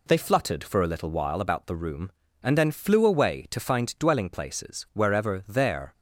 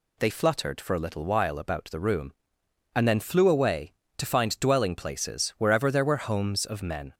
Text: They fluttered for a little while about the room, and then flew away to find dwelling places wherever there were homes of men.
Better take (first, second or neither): second